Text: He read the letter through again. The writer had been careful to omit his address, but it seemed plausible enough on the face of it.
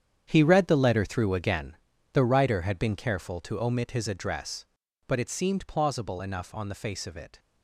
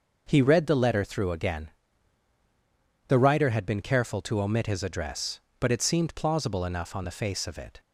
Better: second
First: gets quieter; strong; throughout; 12.5 dB // starts louder than the rest; strong; until 1.2 s; 8.5 dB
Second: starts louder than the rest; noticeable; until 1.2 s; 6 dB

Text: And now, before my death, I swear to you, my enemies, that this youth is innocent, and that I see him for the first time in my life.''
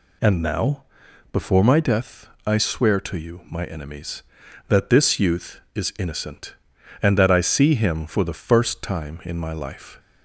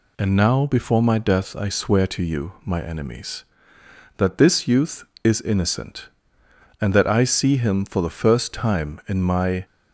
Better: first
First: none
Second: stops before "life"; at 9.6 s

